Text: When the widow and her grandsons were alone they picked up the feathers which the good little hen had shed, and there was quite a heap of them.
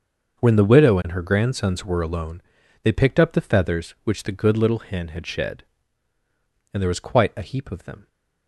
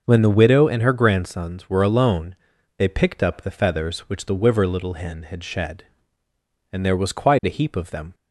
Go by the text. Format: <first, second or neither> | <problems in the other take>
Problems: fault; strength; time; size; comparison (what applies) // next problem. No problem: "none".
first | starts louder than the rest; until 1.0 s; 6 dB; also in the first // pauses between "alone" and "they"; at 2.3 s; 0.40 s long; also in the first // says "wiver" for "good"; at 4.3 s